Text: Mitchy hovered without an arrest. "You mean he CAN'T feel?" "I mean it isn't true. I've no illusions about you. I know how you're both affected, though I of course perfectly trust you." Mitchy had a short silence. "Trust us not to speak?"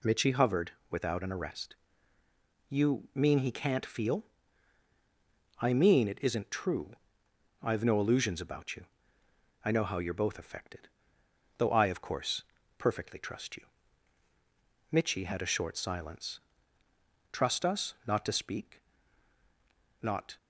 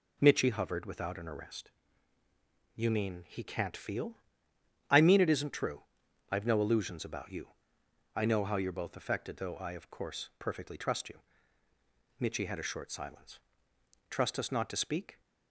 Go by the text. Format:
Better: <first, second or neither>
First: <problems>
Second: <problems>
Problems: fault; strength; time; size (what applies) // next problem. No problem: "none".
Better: second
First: pauses between "hovered" and "without"; slight; at 0.7 s; 0.20 s long // pauses between "course" and "perfectly"; slight; at 12.4 s; 0.36 s long // goes on to say "Not"; slight; from 20.0 s on; 0.36 s long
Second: none